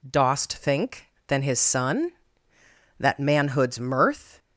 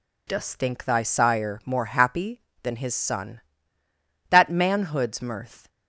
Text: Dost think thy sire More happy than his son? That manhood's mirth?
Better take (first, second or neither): second